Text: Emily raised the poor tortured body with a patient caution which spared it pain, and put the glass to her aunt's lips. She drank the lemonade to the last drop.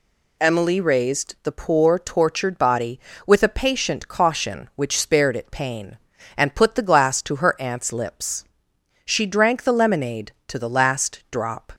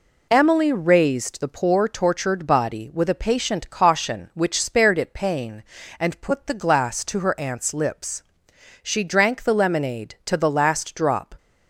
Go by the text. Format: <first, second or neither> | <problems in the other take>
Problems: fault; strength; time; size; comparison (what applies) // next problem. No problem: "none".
neither | none